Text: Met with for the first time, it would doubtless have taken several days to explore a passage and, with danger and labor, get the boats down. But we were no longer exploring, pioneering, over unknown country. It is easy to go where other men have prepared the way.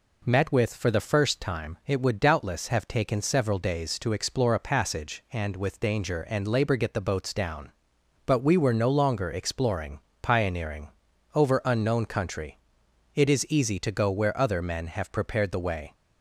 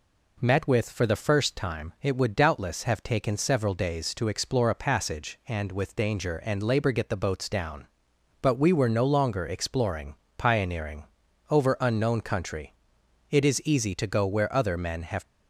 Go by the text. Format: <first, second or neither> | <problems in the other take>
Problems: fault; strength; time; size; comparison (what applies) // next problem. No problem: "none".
first | stops before "prepared the way"; at 15.2 s